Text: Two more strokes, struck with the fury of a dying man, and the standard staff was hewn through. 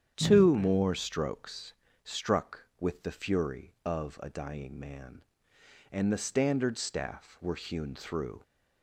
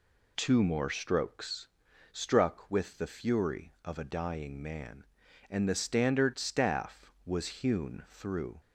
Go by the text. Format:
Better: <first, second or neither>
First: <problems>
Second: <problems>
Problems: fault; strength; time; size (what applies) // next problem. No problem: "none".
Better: second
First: starts louder than the rest; strong; until 1.1 s; 9 dB // says "were" for "was"; at 7.4 s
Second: none